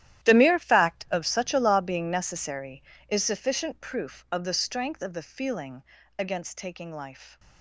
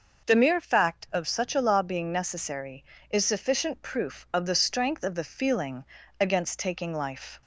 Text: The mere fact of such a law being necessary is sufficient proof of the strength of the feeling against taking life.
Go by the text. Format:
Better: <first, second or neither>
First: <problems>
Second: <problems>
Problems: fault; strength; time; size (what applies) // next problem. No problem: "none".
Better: second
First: gets quieter; strong; throughout; 16 dB // starts louder than the rest; strong; until 1.3 s; 12.5 dB // pauses between "feeling" and "against"; slight; at 5.8 s; 0.34 s long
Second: starts louder than the rest; noticeable; until 1.3 s; 6 dB // pauses between "feeling" and "against"; slight; at 5.8 s; 0.34 s long